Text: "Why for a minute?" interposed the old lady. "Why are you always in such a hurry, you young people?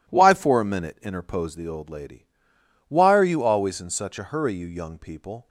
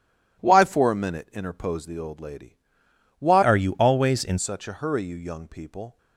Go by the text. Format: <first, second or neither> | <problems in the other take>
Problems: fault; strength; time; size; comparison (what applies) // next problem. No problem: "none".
first | changes voice from "are" to "in"; from 3.4 to 4.3 s; 0.9 s long